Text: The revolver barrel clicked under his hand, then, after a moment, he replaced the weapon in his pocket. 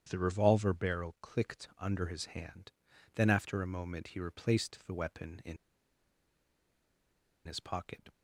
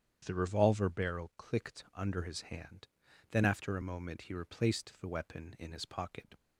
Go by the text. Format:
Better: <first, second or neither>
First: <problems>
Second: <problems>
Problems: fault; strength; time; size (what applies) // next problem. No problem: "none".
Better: second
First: starts louder than the rest; strong; until 1.1 s; 9 dB // pauses between "in" and "his"; strong; at 5.5 s; 1.8 s long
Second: starts louder than the rest; strong; until 1.2 s; 9 dB